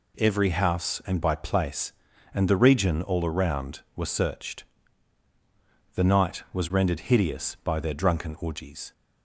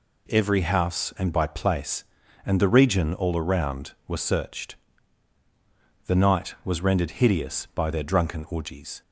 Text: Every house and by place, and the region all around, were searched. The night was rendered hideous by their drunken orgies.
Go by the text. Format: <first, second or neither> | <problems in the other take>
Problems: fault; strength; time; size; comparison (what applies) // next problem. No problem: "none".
neither | none